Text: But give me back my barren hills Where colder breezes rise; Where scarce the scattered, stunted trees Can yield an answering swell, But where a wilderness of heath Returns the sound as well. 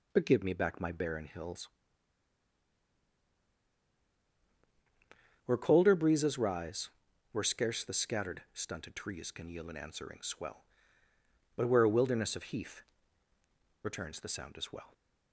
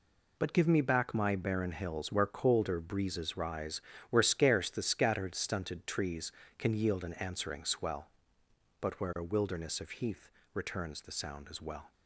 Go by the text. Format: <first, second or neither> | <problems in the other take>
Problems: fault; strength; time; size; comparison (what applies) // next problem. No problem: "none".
second | pauses between "hills" and "Where"; strong; at 1.6 s; 3.7 s long // pauses between "heath" and "Returns"; at 12.8 s; 1.0 s long; slight in the second